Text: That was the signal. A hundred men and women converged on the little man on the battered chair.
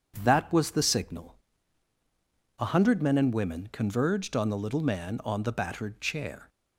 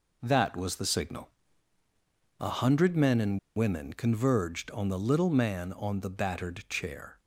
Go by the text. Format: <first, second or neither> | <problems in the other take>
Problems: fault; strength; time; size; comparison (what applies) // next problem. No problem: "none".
first | pauses between "and" and "women"; slight; at 3.3 s; 0.18 s long